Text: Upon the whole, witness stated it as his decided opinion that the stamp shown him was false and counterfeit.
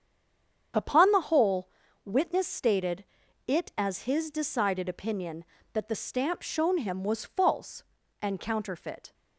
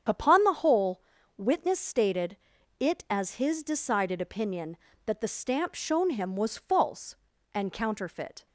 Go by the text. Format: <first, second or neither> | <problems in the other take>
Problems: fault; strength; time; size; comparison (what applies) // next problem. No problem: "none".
second | stays silent before the first word; slight; until 0.7 s; 0.7 s long // starts louder than the rest; strong; until 2.0 s; 7.5 dB; strong in the second // pauses between "stated" and "it"; at 3.0 s; 0.42 s long; also in the second